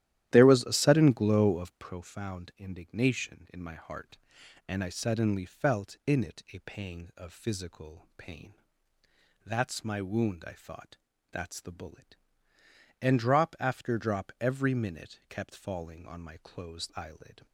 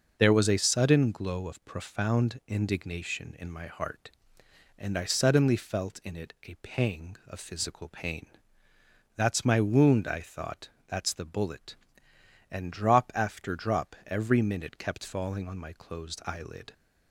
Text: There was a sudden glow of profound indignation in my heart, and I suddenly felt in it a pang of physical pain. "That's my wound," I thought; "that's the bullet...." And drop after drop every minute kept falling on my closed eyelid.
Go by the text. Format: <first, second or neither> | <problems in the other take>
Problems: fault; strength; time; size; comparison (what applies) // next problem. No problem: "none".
second | starts louder than the rest; strong; until 2.0 s; 12.5 dB